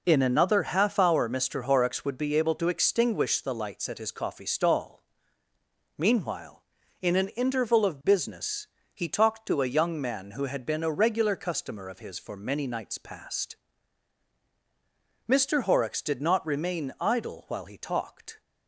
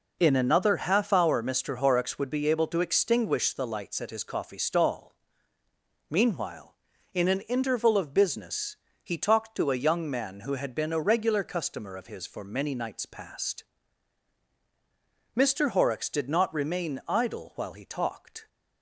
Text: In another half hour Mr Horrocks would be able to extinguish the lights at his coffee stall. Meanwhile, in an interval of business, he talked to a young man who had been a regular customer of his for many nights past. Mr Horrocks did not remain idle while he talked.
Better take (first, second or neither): neither